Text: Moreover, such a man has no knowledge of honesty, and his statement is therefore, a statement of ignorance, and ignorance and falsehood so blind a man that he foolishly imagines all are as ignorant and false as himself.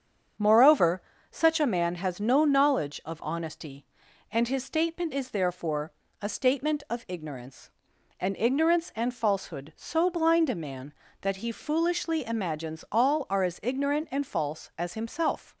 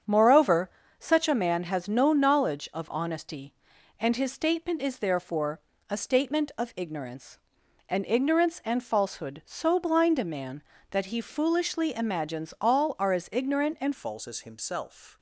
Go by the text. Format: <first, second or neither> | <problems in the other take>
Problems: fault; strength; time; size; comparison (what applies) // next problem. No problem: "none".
first | starts louder than the rest; strong; until 1.3 s; 7.5 dB; strong in the first // changes voice at "false"; from 13.9 s on; 1.2 s long